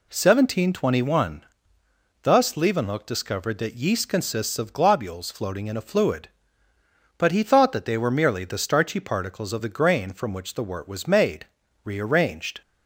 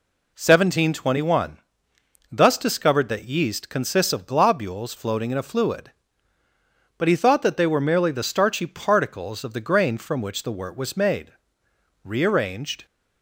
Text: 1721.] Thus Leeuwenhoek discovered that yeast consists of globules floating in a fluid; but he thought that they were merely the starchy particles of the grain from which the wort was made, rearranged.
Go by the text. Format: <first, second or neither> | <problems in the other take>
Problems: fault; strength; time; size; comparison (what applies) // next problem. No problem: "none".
first | skips "Leeuwenhoek"; at 2.5 s